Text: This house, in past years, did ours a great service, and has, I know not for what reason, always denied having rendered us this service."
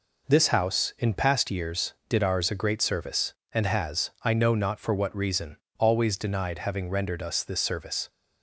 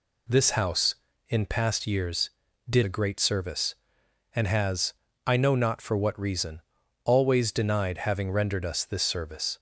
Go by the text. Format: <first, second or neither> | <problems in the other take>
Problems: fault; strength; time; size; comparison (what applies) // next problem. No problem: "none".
first | skips "ours"; at 2.8 s